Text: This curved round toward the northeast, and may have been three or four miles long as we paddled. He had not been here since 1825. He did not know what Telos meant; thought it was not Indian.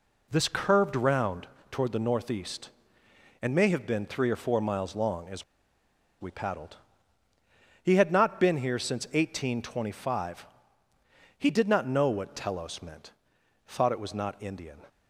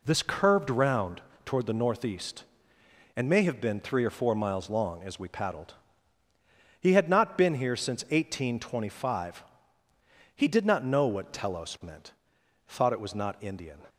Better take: second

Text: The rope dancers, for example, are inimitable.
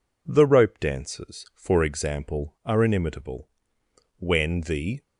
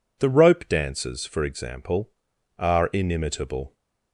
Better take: second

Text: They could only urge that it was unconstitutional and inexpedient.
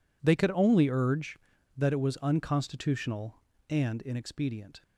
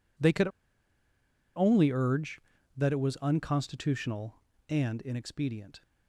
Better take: first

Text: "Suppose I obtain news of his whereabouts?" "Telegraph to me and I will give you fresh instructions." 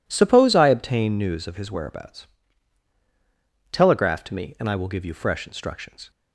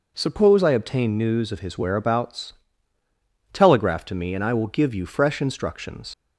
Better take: first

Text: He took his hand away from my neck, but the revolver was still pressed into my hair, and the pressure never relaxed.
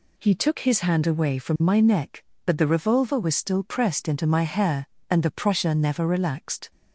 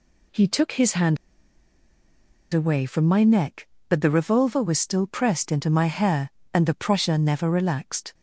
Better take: first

